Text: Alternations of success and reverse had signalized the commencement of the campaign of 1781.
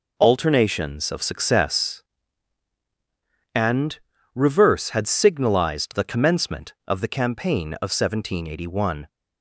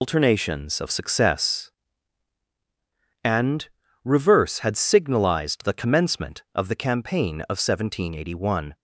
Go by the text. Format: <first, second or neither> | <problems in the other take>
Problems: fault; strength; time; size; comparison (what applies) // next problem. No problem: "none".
first | loses the start of "Alternations"; at 0.0 s; 130 ms // pauses between "and" and "reverse"; slight; at 3.6 s; 0.34 s long; slight in the first